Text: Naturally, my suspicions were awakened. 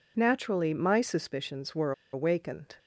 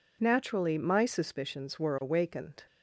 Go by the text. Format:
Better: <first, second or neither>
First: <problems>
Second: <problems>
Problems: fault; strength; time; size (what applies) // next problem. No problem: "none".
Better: second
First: pauses between "were" and "awakened"; slight; at 1.9 s; 0.21 s long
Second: none